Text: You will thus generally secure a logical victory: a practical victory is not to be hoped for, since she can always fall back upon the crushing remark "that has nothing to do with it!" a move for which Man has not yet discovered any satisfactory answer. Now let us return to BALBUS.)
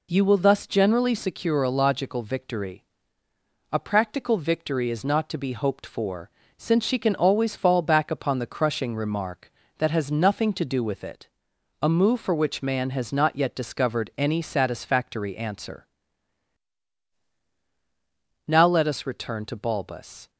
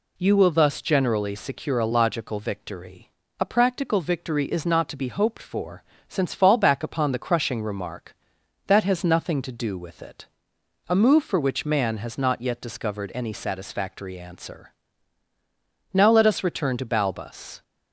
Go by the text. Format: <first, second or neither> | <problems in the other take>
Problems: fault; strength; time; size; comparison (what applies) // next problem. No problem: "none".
first | skips "she can always"; at 6.3 s